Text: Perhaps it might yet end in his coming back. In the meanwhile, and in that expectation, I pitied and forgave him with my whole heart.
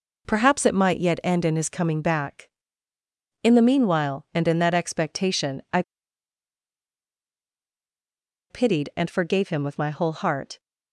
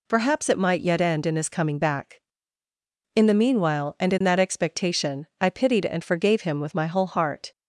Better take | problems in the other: second | pauses between "I" and "pitied"; strong; at 5.8 s; 2.6 s long

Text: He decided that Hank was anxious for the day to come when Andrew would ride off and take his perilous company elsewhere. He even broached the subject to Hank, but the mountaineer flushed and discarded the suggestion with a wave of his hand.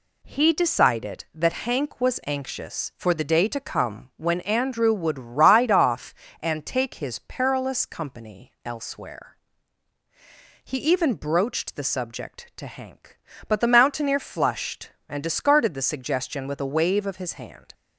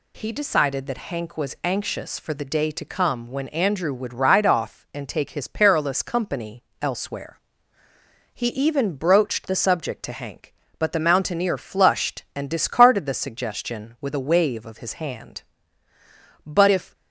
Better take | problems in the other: first | pauses between "company" and "elsewhere"; slight; at 6.6 s; 0.16 s long // goes on to say "But if"; from 16.4 s on; 0.48 s long

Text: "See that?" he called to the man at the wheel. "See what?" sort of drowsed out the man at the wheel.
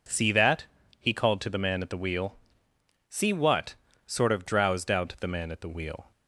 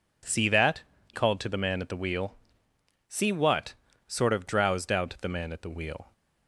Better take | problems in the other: first | skips "he"; at 0.9 s

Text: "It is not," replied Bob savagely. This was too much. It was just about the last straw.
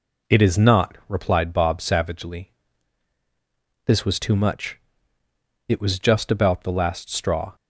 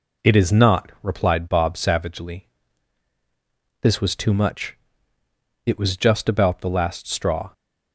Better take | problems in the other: neither | none

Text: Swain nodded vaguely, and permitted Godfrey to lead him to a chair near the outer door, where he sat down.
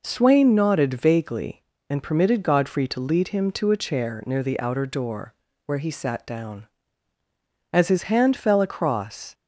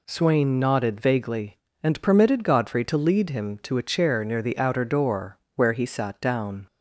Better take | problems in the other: second | goes on to say "As his hand fell across"; from 7.7 s on; 1.6 s long

